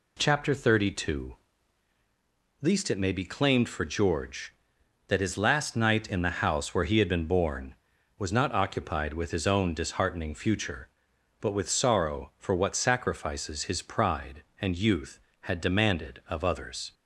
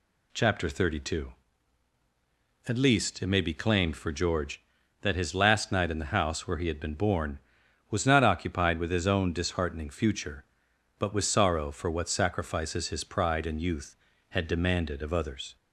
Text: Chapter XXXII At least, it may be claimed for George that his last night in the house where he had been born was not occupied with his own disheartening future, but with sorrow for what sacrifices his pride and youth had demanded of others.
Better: second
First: skips "At"; at 1.9 s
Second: none

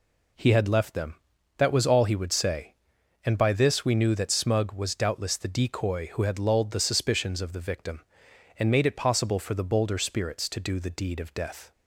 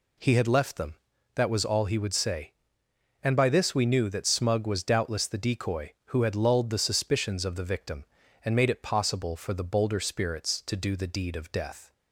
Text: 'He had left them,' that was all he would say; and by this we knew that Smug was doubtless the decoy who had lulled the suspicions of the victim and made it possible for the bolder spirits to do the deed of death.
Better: neither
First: none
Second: none

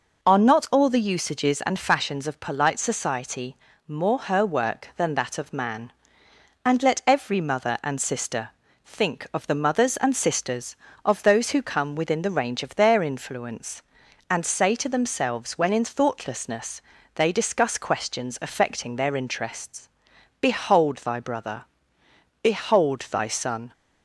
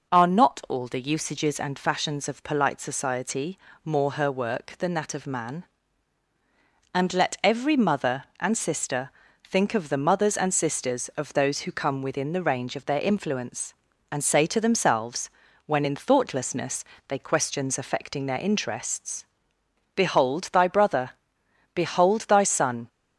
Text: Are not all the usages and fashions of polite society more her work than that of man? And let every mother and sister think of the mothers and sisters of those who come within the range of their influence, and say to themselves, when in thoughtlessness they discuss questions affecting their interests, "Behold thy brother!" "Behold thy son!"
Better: first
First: pauses between "society" and "more"; slight; at 3.5 s; 0.32 s long // pauses between "sister" and "think"; slight; at 8.5 s; 0.34 s long // pauses between "thoughtlessness" and "they"; slight; at 16.8 s; 0.32 s long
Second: pauses between "society" and "more"; slight; at 3.5 s; 0.24 s long // pauses between "sister" and "think"; slight; at 9.1 s; 0.34 s long // pauses between "thoughtlessness" and "they"; slight; at 16.8 s; 0.24 s long // skips "discuss"; at 17.1 s

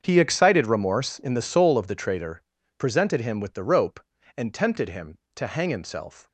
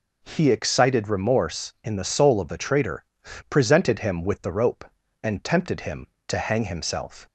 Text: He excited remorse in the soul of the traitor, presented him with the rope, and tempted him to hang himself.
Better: second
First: gets quieter; strong; throughout; 14 dB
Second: none

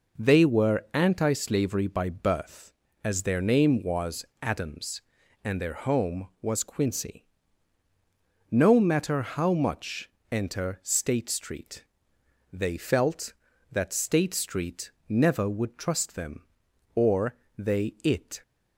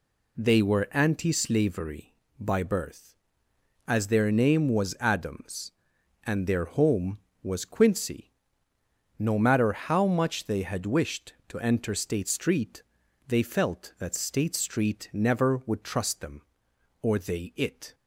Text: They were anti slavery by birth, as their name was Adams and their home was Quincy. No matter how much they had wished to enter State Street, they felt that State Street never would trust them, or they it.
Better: second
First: pauses between "was" and "Adams"; slight; at 4.2 s; 0.16 s long // skips "they had wished to"; at 10.2 s // pauses between "Street" and "never"; slight; at 14.9 s; 0.18 s long // pauses between "or" and "they"; slight; at 17.3 s; 0.24 s long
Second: none

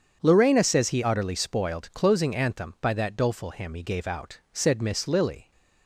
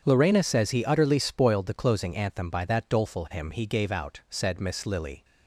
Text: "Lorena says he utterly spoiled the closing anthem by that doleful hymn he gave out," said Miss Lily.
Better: second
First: starts louder than the rest; strong; until 1.2 s; 8 dB // skips "the"; at 1.9 s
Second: starts louder than the rest; strong; until 1.0 s; 8 dB

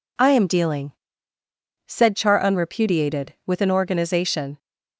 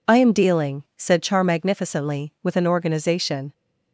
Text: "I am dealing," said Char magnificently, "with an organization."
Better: second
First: says "unrepudiated" for "magnificently"; at 2.3 s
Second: none

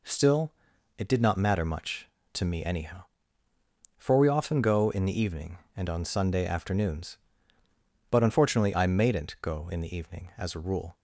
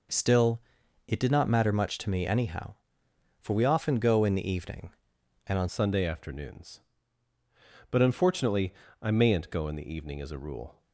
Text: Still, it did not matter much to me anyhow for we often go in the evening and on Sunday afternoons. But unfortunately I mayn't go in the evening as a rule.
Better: first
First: none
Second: changes voice at "Sunday"; from 5.6 s on; 5.2 s long // pauses between "unfortunately" and "I"; slight; at 8.7 s; 0.28 s long

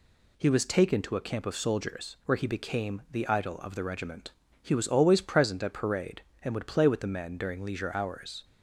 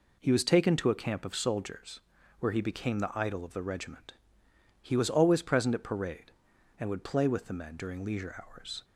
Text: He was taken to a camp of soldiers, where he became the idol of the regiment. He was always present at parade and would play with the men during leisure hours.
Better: neither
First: none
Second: none

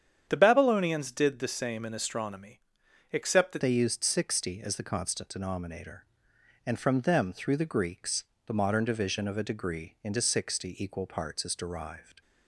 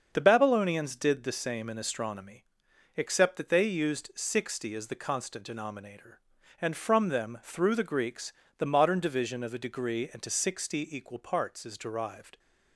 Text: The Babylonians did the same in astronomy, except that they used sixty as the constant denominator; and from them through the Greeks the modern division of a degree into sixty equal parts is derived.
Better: second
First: starts louder than the rest; strong; until 1.3 s; 9 dB // changes voice at "they"; from 3.6 s on; 8.6 s long // pauses between "Greeks" and "the"; slight; at 8.2 s; 0.20 s long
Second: starts louder than the rest; until 1.1 s; 6.5 dB // pauses between "Greeks" and "the"; slight; at 8.3 s; 0.24 s long

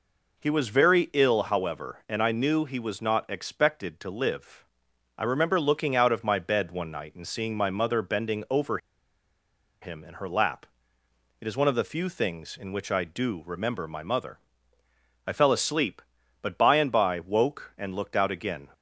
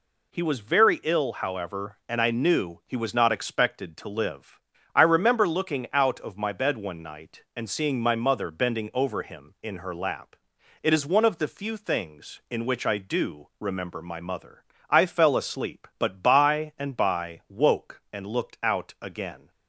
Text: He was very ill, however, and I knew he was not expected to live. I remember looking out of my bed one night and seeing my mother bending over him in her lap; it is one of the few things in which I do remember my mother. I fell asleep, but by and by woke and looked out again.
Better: second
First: pauses between "over" and "him"; at 8.7 s; 1.0 s long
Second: none

